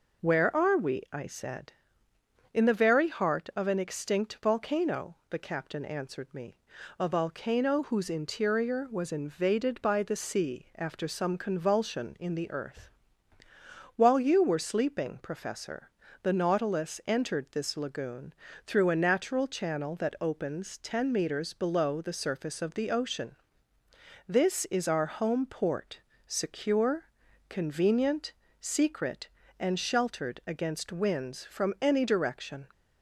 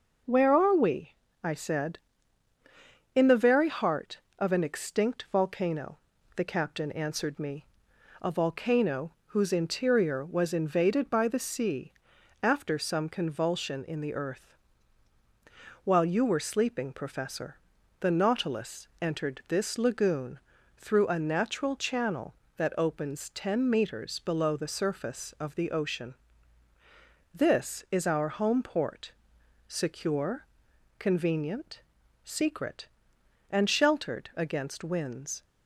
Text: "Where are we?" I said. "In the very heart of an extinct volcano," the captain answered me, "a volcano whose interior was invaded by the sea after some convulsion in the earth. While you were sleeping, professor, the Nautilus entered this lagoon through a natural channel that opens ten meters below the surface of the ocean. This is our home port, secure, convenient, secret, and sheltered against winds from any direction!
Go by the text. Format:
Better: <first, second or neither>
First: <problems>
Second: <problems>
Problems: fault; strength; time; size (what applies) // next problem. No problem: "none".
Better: first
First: pauses between "lagoon" and "through"; slight; at 18.3 s; 0.32 s long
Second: pauses between "sea" and "after"; noticeable; at 11.9 s; 0.52 s long // pauses between "lagoon" and "through"; at 20.3 s; 0.38 s long // stops before "from any direction"; at 35.4 s